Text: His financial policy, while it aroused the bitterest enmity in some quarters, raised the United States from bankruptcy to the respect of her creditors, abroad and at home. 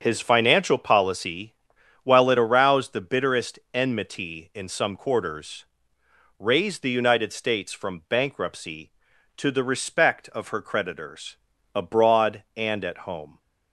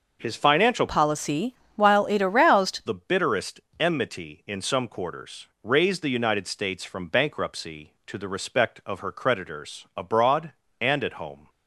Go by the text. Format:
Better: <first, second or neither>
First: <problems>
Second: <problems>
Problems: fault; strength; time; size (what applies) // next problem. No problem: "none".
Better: first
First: starts louder than the rest; strong; until 1.0 s; 7.5 dB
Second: starts louder than the rest; until 1.2 s; 6 dB // changes voice from "policy" to "aroused"; from 0.8 to 2.8 s; 2.0 s long // pauses between "bitterest" and "enmity"; slight; at 3.5 s; 0.20 s long